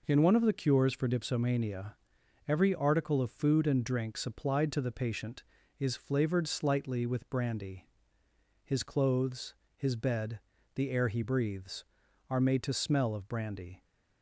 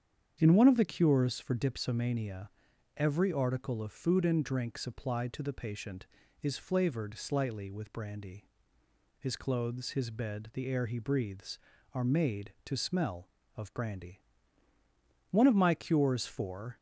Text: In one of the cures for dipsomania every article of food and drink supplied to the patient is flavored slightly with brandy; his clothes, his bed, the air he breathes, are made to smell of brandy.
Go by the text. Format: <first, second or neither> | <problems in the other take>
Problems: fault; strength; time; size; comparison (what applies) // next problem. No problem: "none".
first | starts louder than the rest; strong; until 1.4 s; 8 dB // pauses between "dipsomania" and "every"; at 2.4 s; 0.45 s long; noticeable in the first // goes on to say "One of my cures for"; from 15.3 s on; 1.4 s long